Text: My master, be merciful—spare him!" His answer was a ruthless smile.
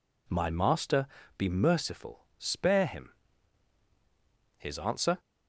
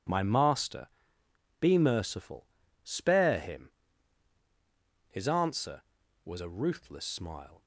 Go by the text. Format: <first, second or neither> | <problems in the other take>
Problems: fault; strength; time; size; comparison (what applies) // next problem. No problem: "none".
second | stops before "was a ruthless smile"; at 5.1 s